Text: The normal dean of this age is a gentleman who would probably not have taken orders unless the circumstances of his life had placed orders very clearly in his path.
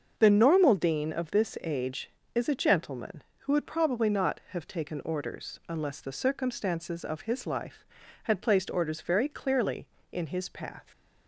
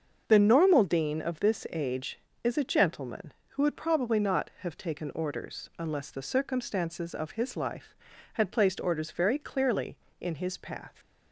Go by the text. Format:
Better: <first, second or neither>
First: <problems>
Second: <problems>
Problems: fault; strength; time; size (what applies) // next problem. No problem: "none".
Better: neither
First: starts louder than the rest; until 1.2 s; 6.5 dB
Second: starts louder than the rest; until 1.2 s; 6.5 dB